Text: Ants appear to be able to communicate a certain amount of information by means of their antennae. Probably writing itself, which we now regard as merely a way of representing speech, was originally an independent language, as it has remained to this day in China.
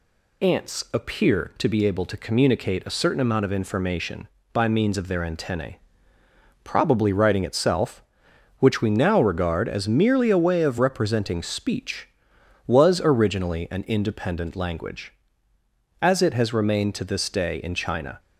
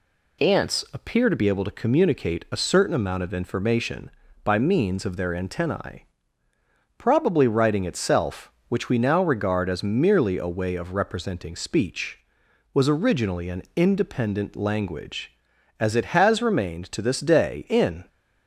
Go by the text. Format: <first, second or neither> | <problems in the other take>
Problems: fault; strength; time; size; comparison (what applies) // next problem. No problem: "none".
first | stops before "China"; at 18.0 s